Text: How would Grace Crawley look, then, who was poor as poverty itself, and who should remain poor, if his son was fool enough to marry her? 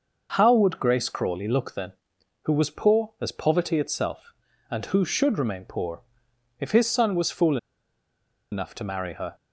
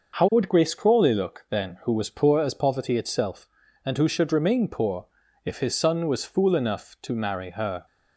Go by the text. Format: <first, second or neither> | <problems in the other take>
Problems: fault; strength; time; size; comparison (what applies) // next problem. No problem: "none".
second | pauses between "fool" and "enough"; noticeable; at 7.5 s; 0.95 s long